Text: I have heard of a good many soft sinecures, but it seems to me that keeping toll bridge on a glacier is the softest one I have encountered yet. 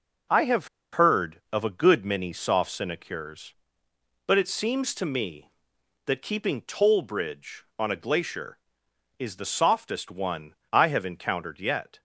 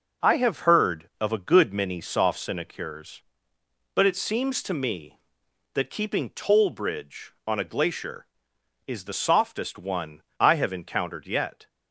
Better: second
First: pauses between "have" and "heard"; slight; at 0.6 s; 0.24 s long // pauses between "one" and "I"; slight; at 10.5 s; 0.16 s long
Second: pauses between "one" and "I"; slight; at 10.2 s; 0.16 s long

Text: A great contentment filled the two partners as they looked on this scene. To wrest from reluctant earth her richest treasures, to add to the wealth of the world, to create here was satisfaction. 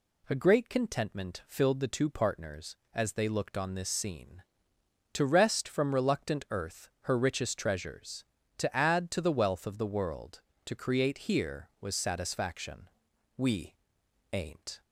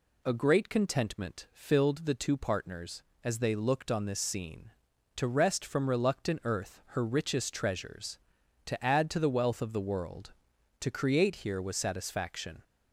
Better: second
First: goes on to say "We ain't"; from 13.3 s on; 1.4 s long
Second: none

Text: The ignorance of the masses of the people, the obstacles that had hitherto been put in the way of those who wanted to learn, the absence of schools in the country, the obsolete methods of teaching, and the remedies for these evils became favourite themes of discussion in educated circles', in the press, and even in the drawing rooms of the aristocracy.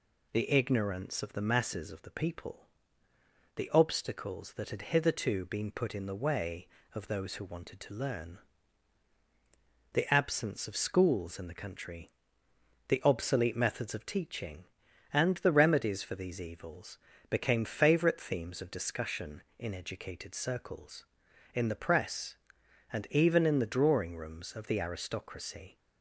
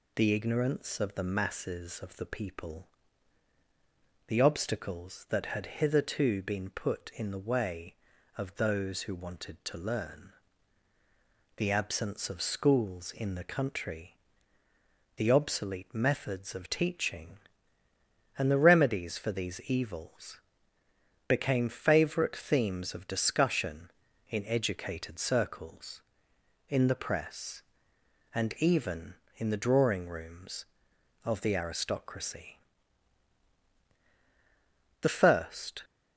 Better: first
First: pauses between "evils" and "became"; slight; at 16.9 s; 0.32 s long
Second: pauses between "evils" and "became"; noticeable; at 20.4 s; 0.86 s long // goes on to say "The first"; noticeable; from 35.0 s on; 0.83 s long

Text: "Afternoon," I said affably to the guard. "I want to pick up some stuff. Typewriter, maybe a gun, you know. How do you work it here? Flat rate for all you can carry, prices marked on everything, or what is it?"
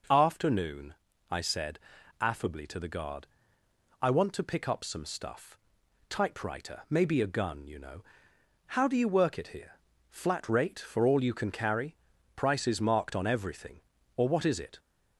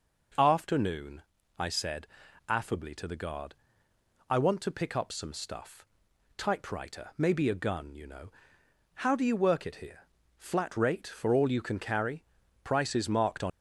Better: first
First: pauses between "said" and "affably"; at 1.7 s; 0.42 s long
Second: pauses between "said" and "affably"; at 2.0 s; 0.42 s long // stops before "everything or what is it"; at 13.5 s

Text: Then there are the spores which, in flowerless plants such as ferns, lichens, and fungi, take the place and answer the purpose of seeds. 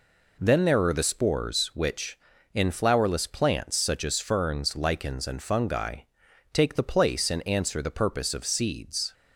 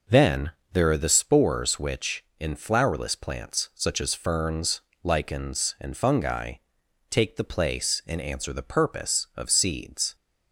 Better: first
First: none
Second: starts louder than the rest; noticeable; until 1.3 s; 5.5 dB // pauses between "Then" and "there"; slight; at 0.5 s; 0.22 s long

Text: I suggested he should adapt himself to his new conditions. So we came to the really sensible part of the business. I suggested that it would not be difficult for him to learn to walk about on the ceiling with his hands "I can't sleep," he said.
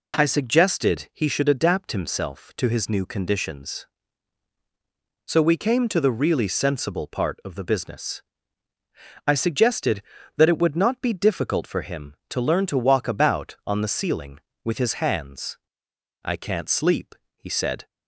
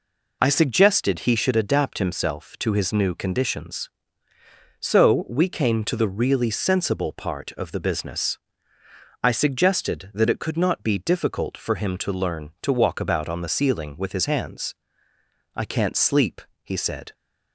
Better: first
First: pauses between "hands" and "I"; noticeable; at 15.5 s; 0.66 s long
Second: says "could" for "would"; at 10.4 s // pauses between "hands" and "I"; noticeable; at 14.7 s; 0.82 s long

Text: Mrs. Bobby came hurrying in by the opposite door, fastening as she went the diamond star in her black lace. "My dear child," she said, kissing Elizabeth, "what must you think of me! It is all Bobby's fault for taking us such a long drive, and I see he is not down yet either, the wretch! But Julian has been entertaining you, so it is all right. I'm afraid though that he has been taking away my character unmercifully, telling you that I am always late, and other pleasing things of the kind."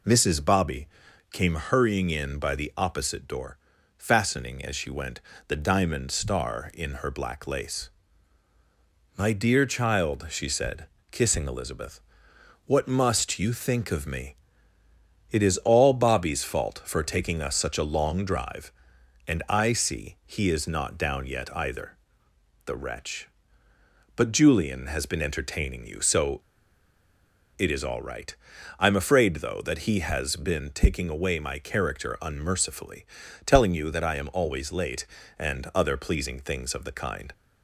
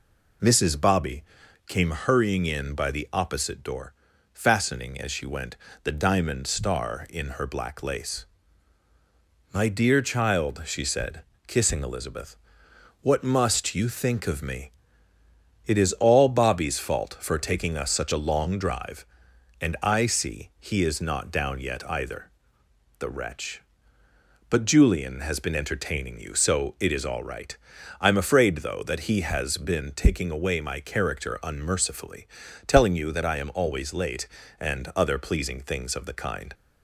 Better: second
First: pauses between "Bobby" and "came"; noticeable; at 0.8 s; 0.46 s long // pauses between "went" and "the"; slight; at 5.2 s; 0.28 s long // pauses between "so" and "it"; at 26.4 s; 1.1 s long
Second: pauses between "Bobby" and "came"; noticeable; at 1.2 s; 0.46 s long // pauses between "went" and "the"; slight; at 5.5 s; 0.28 s long

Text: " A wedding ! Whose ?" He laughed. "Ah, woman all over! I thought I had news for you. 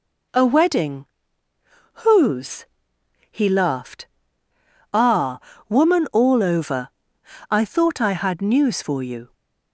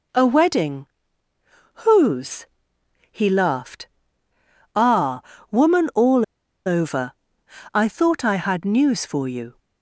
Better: first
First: none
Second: pauses between "all" and "over"; at 6.2 s; 0.42 s long

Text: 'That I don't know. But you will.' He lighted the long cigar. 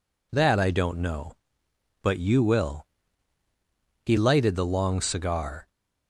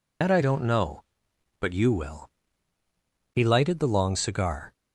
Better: first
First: none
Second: loses the start of "That"; at 0.2 s; 90 ms

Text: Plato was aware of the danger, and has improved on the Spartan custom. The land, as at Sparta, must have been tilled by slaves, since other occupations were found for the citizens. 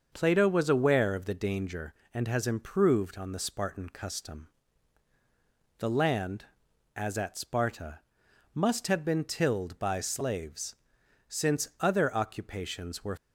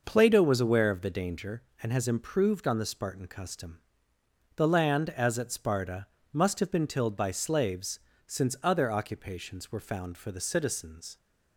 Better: second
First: starts louder than the rest; until 1.1 s; 6.5 dB // stops before "found for the citizens"; at 13.1 s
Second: none

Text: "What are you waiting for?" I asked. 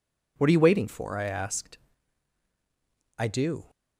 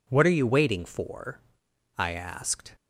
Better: second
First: goes on to say "I do"; from 3.1 s on; 0.52 s long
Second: none

